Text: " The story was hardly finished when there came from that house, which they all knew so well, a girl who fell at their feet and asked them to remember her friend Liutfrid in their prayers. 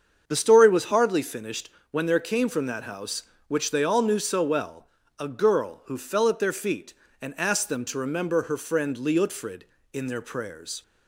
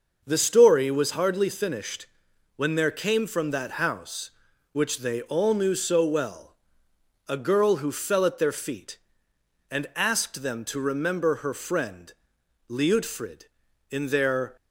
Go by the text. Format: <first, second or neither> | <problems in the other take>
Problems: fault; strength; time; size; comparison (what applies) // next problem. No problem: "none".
first | starts louder than the rest; noticeable; until 1.2 s; 6 dB; also in the first // pauses between "finished" and "when"; noticeable; at 2.0 s; 0.50 s long; slight in the first // pauses between "friend" and "Liutfrid"; noticeable; at 12.1 s; 0.56 s long // stops before "prayers"; at 14.5 s